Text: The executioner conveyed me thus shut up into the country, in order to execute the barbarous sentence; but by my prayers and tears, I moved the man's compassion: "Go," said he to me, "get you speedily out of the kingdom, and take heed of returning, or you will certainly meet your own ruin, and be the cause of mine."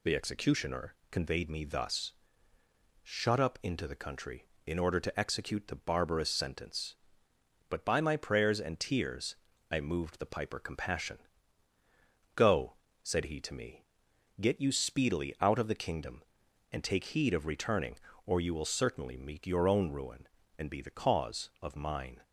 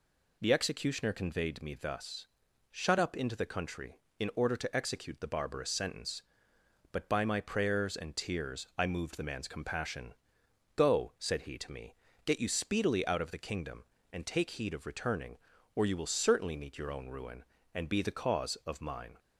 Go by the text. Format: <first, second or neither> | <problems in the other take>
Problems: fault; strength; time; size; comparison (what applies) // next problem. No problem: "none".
second | pauses between "executioner" and "conveyed"; slight; at 0.9 s; 0.16 s long // pauses between "thus" and "shut"; noticeable; at 2.1 s; 0.94 s long; also in the second // says "piper" for "man's"; at 10.2 s